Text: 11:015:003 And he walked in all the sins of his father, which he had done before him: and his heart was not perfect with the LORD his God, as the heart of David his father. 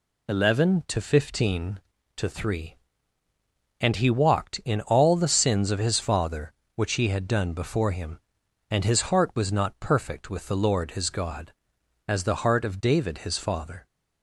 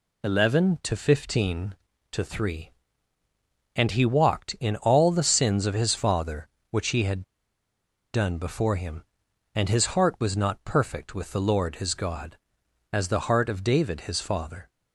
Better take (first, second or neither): first